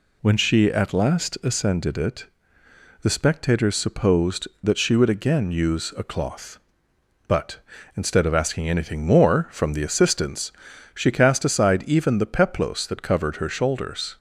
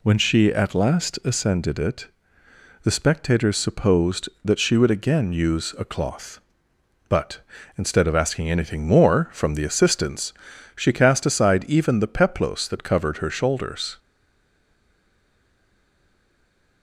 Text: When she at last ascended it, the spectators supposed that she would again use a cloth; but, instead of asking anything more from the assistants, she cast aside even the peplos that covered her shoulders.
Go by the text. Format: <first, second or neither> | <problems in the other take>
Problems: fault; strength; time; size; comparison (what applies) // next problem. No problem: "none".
first | stays silent after the last word; strong; from 13.9 s on; 2.9 s long